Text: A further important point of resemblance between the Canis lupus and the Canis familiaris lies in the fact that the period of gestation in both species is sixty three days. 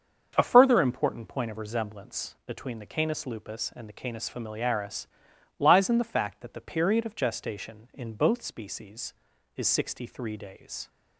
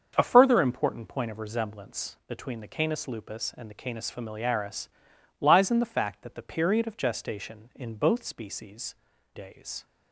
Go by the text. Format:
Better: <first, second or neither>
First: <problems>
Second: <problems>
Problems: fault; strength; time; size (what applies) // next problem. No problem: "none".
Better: first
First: starts louder than the rest; until 1.3 s; 7 dB // pauses between "familiaris" and "lies"; noticeable; at 5.0 s; 0.52 s long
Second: starts louder than the rest; until 1.1 s; 7 dB // pauses between "familiaris" and "lies"; noticeable; at 4.8 s; 0.52 s long // skips "is sixty three"; at 9.1 s